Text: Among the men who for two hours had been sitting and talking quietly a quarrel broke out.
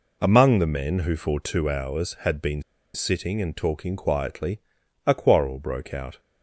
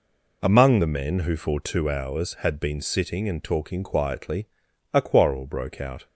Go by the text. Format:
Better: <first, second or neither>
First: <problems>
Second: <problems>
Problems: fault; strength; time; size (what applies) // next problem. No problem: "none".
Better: second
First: pauses between "been" and "sitting"; slight; at 2.6 s; 0.32 s long // pauses between "quietly" and "a"; noticeable; at 4.5 s; 0.46 s long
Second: pauses between "quietly" and "a"; noticeable; at 4.4 s; 0.46 s long